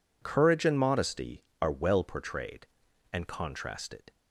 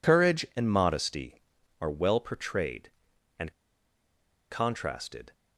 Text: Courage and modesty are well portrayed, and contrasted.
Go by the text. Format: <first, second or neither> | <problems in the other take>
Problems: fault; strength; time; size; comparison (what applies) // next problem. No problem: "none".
first | pauses between "and" and "contrasted"; at 3.5 s; 1.0 s long